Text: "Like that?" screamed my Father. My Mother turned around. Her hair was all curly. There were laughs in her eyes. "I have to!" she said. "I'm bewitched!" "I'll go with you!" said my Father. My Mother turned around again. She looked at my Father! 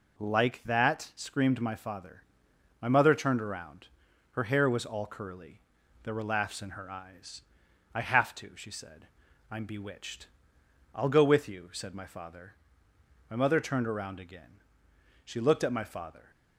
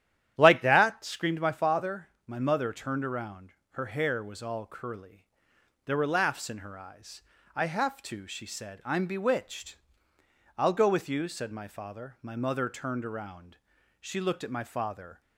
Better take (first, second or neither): first